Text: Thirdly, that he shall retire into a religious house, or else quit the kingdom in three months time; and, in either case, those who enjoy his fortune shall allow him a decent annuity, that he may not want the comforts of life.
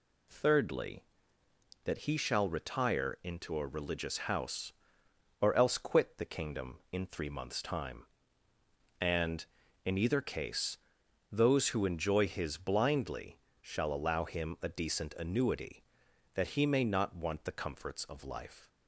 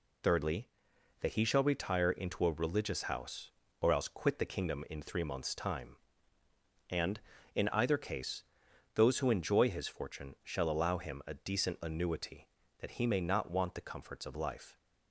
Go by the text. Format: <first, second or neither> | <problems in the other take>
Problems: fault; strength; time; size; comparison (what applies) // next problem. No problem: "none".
second | says "blindly" for "fortune"; at 12.5 s